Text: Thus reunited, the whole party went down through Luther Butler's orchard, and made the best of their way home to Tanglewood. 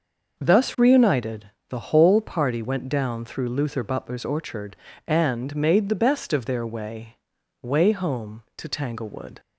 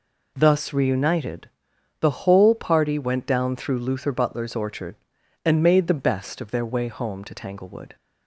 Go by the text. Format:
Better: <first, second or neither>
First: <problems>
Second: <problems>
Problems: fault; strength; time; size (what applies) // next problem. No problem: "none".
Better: second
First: says "way" twice; at 7.6 s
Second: none